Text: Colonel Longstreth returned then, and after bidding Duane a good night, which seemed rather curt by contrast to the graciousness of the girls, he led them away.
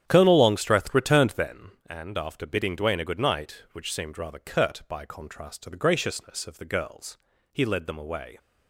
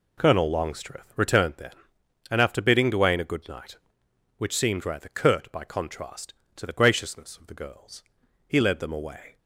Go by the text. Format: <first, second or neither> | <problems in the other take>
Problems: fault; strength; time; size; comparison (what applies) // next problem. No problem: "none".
second | starts louder than the rest; strong; until 1.7 s; 9.5 dB